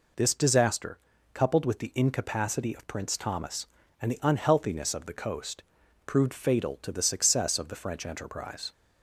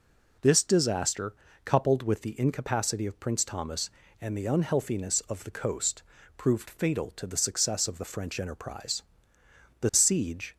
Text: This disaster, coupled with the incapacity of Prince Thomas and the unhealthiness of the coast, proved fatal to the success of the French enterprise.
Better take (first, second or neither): first